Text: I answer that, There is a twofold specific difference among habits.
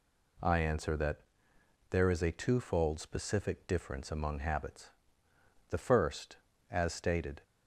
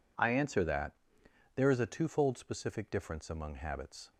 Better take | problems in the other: second | goes on to say "The first as stated"; strong; from 5.6 s on; 1.7 s long

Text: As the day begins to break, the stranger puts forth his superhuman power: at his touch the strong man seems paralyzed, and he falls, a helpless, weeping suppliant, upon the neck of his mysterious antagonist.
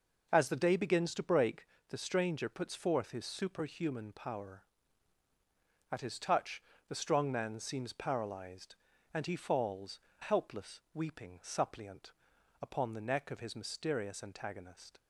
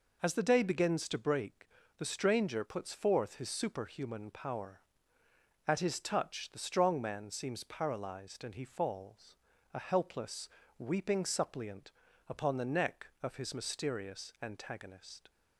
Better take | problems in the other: second | pauses between "touch" and "the"; slight; at 6.6 s; 0.28 s long // skips "a"; at 10.1 s

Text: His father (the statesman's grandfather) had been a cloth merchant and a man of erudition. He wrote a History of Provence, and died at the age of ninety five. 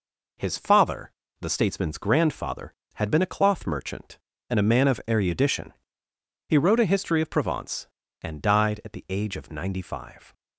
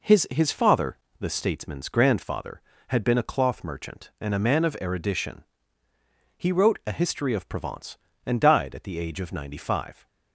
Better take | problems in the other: first | says "His" twice; at 0.3 s

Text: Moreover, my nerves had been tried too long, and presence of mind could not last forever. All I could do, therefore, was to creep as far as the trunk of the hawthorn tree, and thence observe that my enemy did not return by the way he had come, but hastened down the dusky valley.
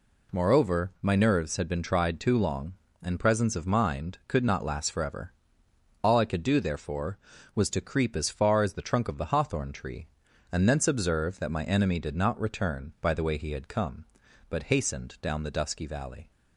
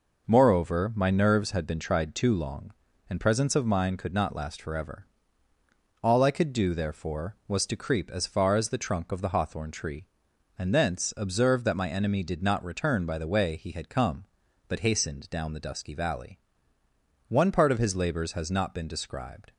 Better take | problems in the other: first | goes on to say "One part of his labors has not been described"; strong; from 17.2 s on; 2.2 s long

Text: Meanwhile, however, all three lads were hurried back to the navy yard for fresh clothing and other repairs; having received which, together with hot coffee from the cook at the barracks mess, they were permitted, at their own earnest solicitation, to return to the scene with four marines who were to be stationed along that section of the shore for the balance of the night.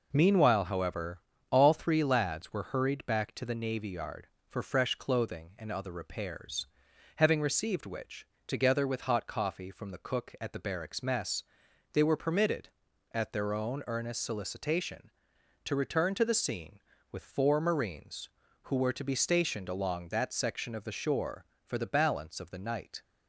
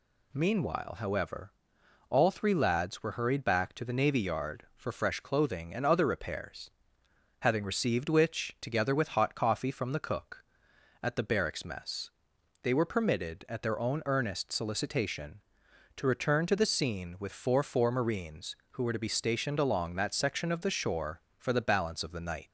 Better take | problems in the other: first | says "four" twice; at 17.6 s

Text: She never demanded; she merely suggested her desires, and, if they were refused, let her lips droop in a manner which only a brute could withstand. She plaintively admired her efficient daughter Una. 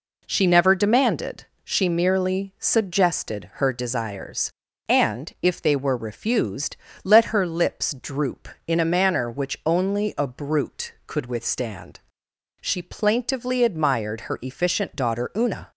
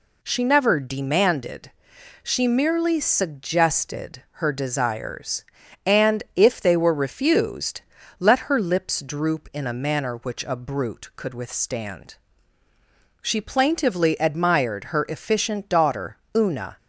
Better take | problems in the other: first | skips "only"; at 10.4 s // pauses between "daughter" and "Una"; slight; at 16.1 s; 0.18 s long

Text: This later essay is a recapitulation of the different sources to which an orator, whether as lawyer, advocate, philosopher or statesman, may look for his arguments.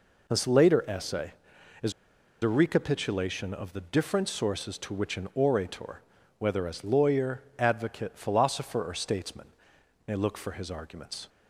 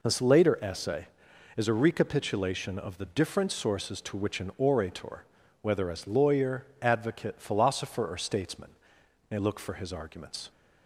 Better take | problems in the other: second | pauses between "is" and "a"; noticeable; at 1.9 s; 0.49 s long

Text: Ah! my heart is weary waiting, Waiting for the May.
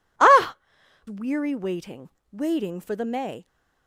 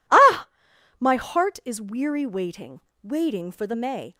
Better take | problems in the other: second | skips "my heart is"; at 0.8 s

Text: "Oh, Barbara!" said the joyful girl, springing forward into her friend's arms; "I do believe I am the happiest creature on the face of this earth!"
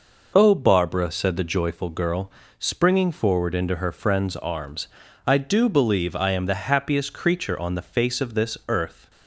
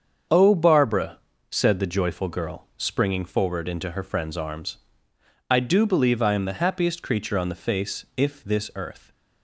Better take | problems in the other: first | starts louder than the rest; until 1.6 s; 7 dB // says "if" for "of"; at 8.1 s

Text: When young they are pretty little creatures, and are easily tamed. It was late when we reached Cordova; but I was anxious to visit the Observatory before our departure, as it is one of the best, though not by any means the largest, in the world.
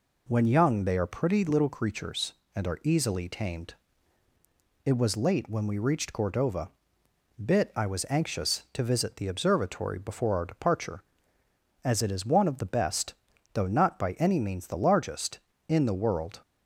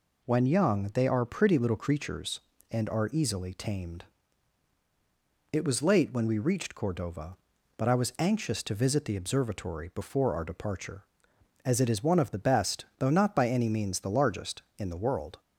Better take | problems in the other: second | says "bit" for "but"; at 7.4 s

